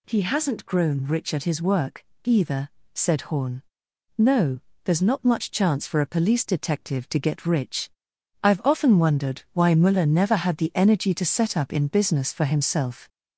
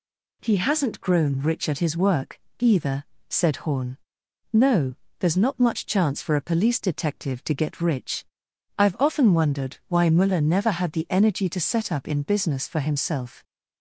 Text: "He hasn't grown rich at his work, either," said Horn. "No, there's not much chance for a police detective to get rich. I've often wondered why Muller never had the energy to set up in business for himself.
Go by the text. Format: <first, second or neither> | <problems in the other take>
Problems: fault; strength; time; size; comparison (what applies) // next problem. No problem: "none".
second | gets louder; slight; throughout; 2.5 dB